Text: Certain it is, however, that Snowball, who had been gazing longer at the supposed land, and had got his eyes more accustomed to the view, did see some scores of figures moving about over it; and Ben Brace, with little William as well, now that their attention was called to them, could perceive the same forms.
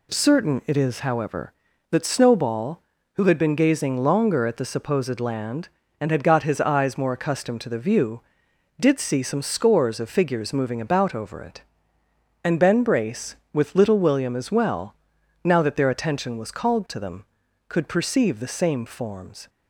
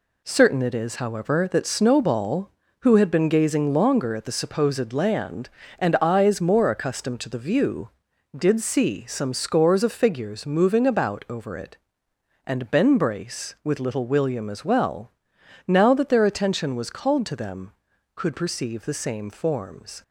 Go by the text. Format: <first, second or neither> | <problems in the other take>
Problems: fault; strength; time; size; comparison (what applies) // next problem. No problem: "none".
first | skips "had got his"; at 5.9 s